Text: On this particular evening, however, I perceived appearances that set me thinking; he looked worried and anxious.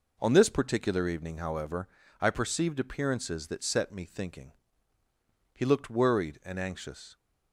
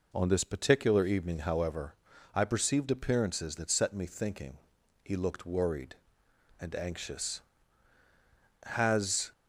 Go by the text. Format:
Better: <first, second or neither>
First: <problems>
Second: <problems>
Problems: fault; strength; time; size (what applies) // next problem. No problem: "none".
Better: first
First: none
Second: goes on to say "Has"; noticeable; from 8.6 s on; 0.68 s long